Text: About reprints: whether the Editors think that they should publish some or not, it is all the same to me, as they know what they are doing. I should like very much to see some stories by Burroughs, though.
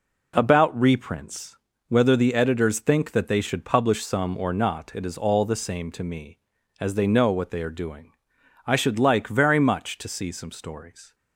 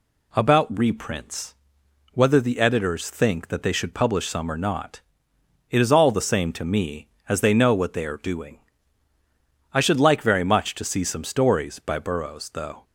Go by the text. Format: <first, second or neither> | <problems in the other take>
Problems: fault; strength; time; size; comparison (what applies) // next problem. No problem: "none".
second | stops before "by Burroughs though"; at 11.1 s